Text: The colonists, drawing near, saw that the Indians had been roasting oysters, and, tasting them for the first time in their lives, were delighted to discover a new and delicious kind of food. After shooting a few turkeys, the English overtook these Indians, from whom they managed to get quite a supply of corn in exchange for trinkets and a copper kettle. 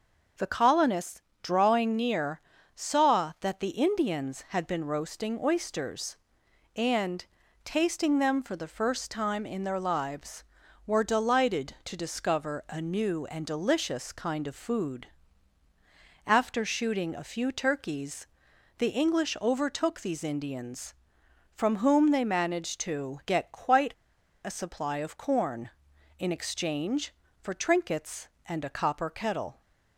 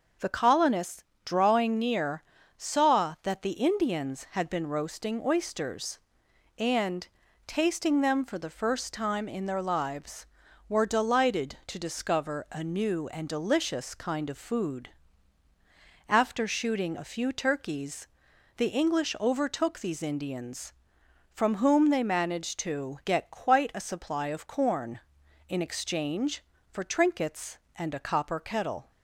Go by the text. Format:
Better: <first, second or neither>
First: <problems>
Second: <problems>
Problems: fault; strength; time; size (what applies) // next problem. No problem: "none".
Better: second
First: starts louder than the rest; until 1.6 s; 6.5 dB // pauses between "quite" and "a"; noticeable; at 23.9 s; 0.51 s long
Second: starts louder than the rest; until 1.4 s; 6.5 dB